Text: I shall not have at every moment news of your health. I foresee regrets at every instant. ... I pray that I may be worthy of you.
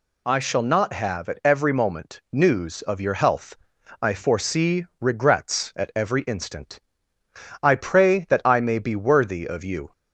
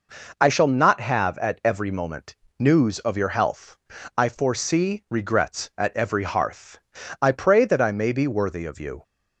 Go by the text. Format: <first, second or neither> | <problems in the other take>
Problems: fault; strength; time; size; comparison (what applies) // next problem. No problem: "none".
first | pauses between "moment" and "news"; slight; at 2.3 s; 0.24 s long // says "hearth" for "instant"; at 6.2 s